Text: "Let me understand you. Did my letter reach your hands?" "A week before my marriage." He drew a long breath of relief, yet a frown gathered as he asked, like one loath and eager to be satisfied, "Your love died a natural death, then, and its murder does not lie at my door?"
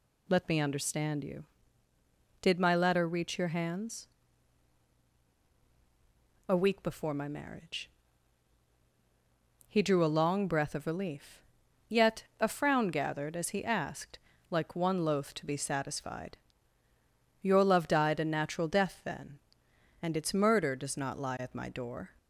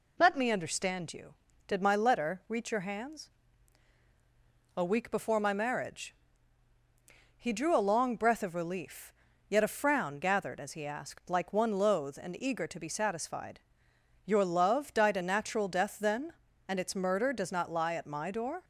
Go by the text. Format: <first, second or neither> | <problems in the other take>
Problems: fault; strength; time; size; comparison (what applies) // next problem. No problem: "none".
second | pauses between "yet" and "a"; slight; at 12.2 s; 0.16 s long // skips "and eager"; at 15.3 s